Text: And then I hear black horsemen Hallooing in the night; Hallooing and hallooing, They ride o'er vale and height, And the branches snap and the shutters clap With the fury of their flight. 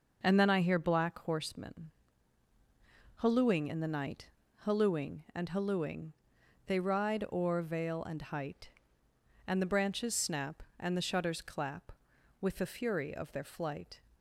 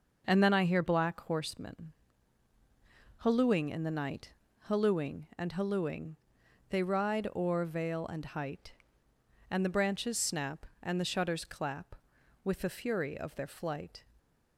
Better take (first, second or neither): neither